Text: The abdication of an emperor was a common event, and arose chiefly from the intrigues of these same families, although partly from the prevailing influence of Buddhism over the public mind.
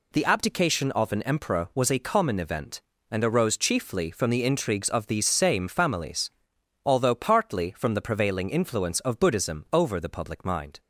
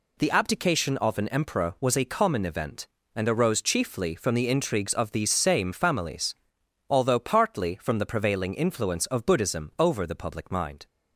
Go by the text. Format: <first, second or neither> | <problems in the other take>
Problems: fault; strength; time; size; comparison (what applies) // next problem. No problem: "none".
neither | none